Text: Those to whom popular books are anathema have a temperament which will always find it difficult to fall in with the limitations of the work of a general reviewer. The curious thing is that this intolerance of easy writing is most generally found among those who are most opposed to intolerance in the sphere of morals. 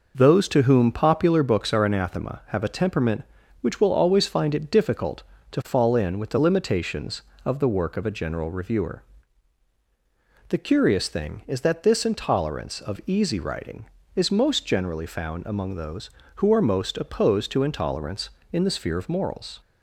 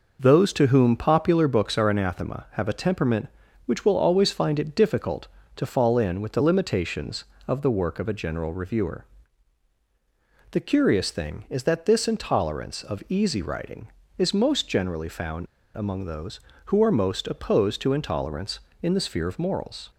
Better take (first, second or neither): first